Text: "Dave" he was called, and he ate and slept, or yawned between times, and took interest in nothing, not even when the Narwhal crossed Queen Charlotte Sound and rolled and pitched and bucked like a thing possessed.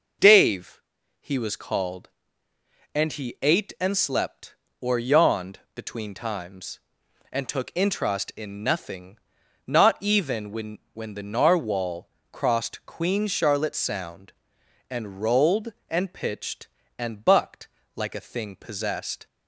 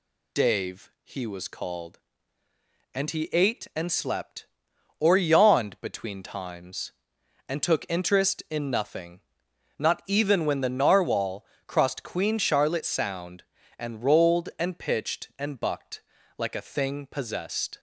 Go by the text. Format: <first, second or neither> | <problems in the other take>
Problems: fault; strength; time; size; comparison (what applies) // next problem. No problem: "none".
second | pauses between "Dave" and "he"; slight; at 0.8 s; 0.36 s long // says "when" twice; at 10.9 s // pauses between "Narwhal" and "crossed"; slight; at 12.1 s; 0.22 s long; slight in the second // pauses between "bucked" and "like"; slight; at 17.6 s; 0.28 s long; slight in the second